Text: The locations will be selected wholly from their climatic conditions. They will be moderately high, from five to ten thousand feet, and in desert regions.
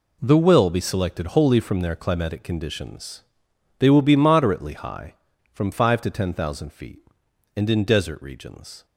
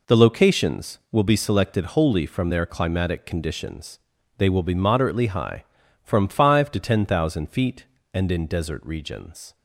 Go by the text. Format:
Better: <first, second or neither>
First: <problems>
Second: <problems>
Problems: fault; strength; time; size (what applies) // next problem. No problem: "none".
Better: second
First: skips "locations"; at 0.3 s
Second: none